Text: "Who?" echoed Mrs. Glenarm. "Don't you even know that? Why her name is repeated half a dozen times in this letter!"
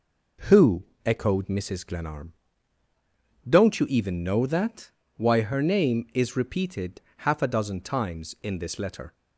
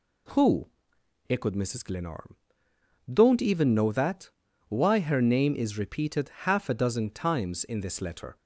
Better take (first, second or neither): first